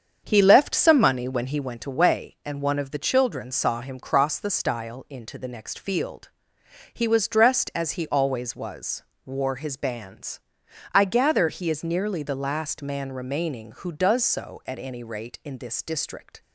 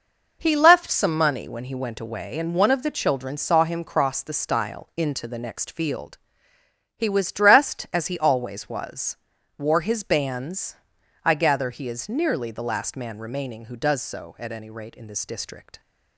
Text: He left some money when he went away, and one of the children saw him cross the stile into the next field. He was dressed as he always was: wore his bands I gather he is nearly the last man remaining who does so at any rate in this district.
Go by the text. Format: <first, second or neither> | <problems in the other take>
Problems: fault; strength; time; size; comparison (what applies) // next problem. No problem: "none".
second | starts louder than the rest; strong; until 1.6 s; 7.5 dB // pauses between "bands" and "I"; noticeable; at 10.4 s; 0.52 s long; noticeable in the second